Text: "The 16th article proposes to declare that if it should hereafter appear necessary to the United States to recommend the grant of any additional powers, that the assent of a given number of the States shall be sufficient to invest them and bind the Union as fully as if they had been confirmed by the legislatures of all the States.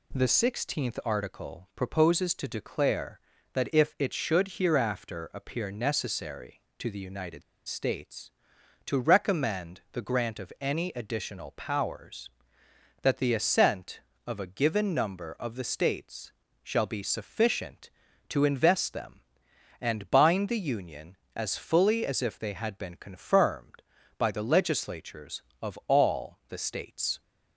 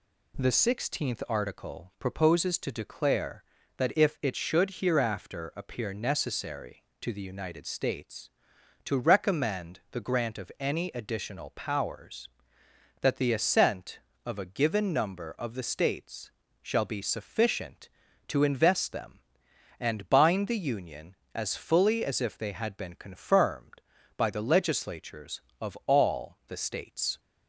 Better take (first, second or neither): second